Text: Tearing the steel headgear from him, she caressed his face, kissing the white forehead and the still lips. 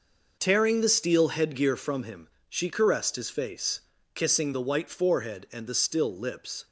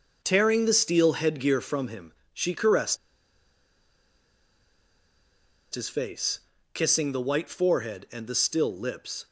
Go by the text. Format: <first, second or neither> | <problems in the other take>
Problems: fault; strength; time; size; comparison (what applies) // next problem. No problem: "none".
first | pauses between "caressed" and "his"; strong; at 2.9 s; 2.7 s long